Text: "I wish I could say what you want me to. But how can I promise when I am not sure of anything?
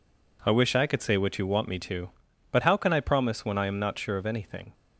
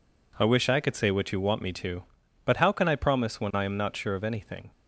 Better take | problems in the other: neither | none

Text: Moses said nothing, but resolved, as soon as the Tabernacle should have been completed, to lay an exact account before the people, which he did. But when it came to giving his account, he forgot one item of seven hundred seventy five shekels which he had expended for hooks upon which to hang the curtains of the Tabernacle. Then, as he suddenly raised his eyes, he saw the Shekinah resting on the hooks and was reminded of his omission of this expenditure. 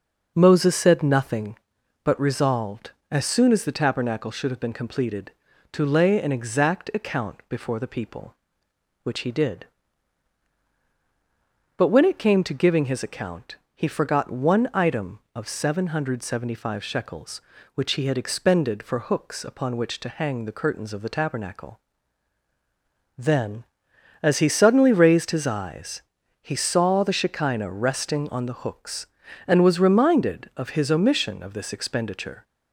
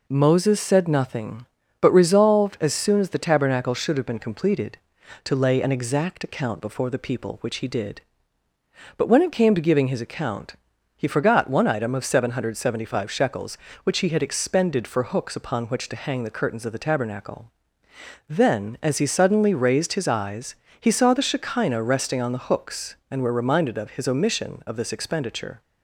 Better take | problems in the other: first | says "were" for "was"; at 23.2 s

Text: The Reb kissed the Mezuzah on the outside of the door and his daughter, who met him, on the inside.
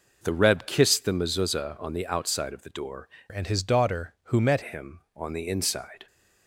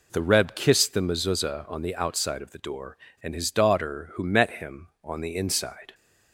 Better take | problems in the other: second | changes voice from "and" to "met"; from 3.2 to 4.6 s; 1.4 s long

